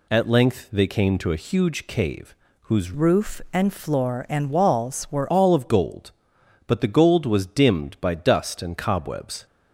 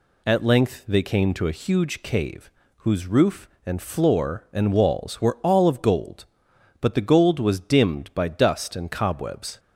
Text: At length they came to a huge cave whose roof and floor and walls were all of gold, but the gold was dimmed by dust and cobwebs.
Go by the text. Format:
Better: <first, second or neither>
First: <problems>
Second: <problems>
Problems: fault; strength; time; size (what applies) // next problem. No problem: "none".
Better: second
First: pauses between "cave" and "whose"; slight; at 2.3 s; 0.26 s long // changes voice from "roof" to "were"; from 2.9 to 5.3 s; 2.4 s long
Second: pauses between "cave" and "whose"; slight; at 2.5 s; 0.26 s long